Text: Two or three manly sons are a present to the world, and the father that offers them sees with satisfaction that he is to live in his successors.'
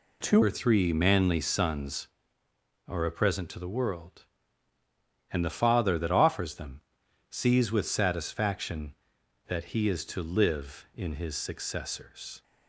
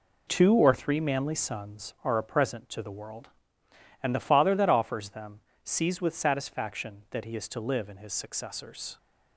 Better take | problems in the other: second | changes voice at "or"; from 0.4 s on; 12.0 s long // pauses between "them" and "sees"; noticeable; at 6.8 s; 0.50 s long; slight in the second

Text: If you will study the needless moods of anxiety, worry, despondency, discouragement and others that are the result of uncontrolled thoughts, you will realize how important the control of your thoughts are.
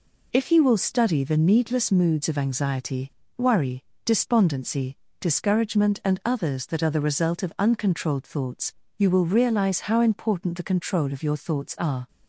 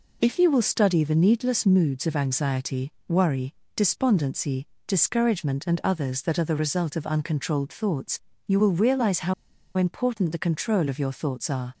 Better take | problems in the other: first | pauses between "how" and "important"; at 9.3 s; 0.43 s long

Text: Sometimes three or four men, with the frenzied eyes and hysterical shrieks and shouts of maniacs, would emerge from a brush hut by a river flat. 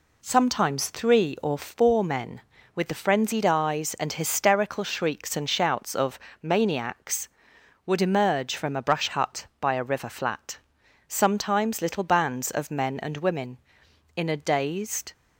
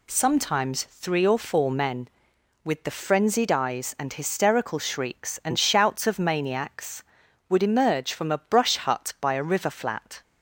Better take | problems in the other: second | pauses between "of" and "maniacs"; slight; at 6.1 s; 0.24 s long // goes on to say "Sometimes little bands of men and women in a dazed"; strong; from 11.0 s on; 4.0 s long

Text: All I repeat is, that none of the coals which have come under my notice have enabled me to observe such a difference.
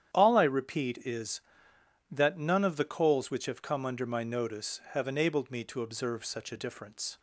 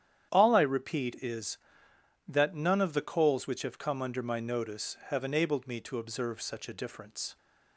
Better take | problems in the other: neither | starts louder than the rest; strong; the same in both

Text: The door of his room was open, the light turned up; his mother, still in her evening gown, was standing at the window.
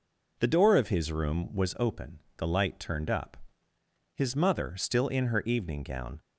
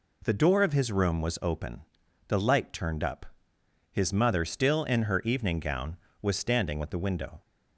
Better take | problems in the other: second | stops before "was standing at the window"; at 6.1 s

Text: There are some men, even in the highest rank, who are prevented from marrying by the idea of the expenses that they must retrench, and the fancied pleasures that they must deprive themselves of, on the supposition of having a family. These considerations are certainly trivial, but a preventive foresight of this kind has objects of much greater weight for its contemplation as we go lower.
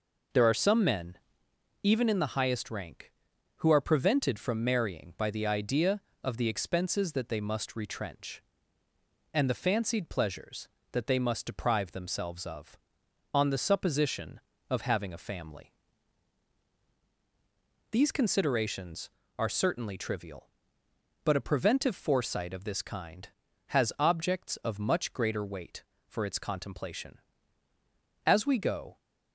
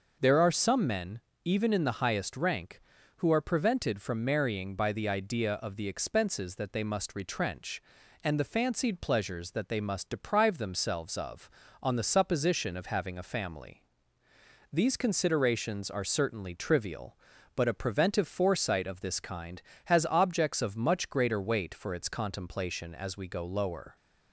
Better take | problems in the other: second | stops before "lower"; at 28.9 s

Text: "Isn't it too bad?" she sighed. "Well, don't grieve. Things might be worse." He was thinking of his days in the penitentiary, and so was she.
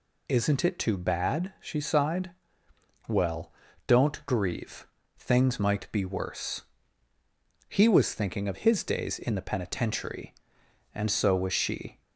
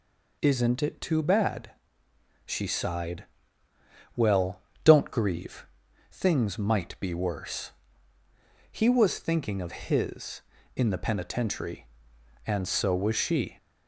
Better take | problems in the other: first | skips "days"; at 10.5 s

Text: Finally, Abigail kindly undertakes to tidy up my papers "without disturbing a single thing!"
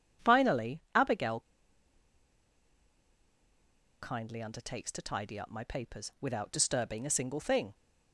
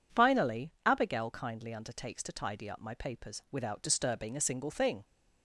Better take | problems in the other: second | pauses between "Abigail" and "kindly"; strong; at 1.4 s; 2.6 s long

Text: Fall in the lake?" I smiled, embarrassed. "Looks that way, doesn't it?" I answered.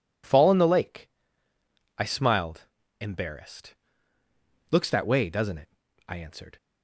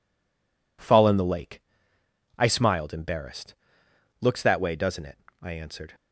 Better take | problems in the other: first | stays silent before the first word; slight; until 0.7 s; 0.7 s long

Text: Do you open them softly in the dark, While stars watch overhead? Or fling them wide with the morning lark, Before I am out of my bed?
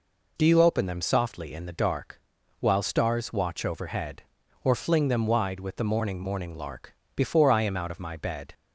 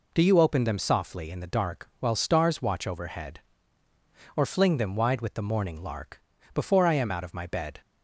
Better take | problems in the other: second | says "morning" twice; at 6.1 s

